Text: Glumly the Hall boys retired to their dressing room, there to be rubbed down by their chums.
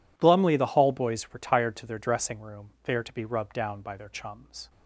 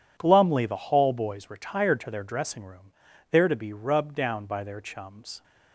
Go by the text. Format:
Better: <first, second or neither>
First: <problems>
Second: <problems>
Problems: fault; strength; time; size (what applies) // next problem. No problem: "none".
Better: neither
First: none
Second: none